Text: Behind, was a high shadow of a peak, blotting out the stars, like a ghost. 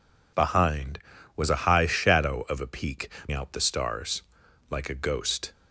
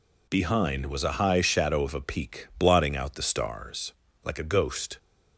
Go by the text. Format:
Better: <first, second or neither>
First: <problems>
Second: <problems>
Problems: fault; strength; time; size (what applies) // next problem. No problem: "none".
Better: second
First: skips "blotting"; at 3.2 s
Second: none